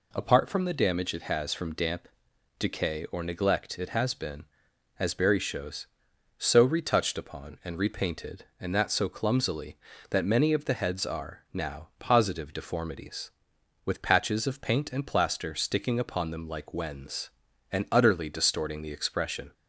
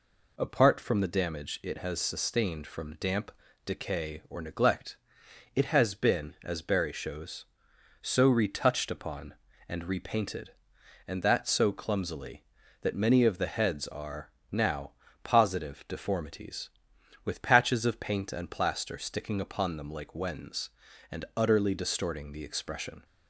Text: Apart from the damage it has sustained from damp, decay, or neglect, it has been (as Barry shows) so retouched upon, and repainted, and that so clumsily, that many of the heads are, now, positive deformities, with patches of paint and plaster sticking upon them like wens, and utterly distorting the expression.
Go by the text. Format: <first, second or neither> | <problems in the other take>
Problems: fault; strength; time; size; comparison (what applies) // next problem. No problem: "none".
second | skips "sustained"; at 1.5 s